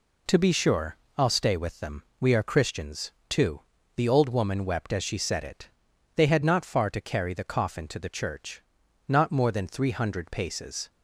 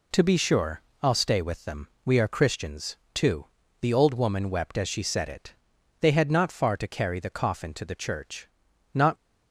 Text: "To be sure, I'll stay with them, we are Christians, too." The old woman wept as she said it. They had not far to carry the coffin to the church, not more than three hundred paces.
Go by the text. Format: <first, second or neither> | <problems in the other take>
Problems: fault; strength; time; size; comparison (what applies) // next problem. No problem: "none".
first | stops before "more than three hundred paces"; at 9.1 s